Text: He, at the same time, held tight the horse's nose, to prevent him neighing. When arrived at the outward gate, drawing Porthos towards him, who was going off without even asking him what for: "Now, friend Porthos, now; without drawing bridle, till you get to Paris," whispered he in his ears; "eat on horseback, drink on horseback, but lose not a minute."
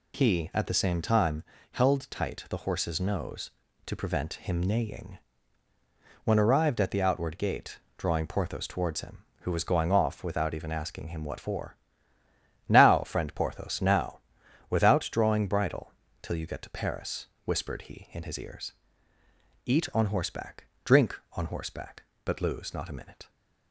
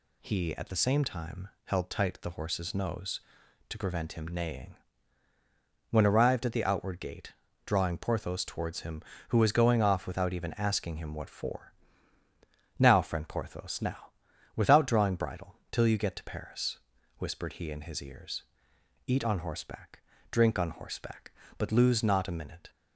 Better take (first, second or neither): neither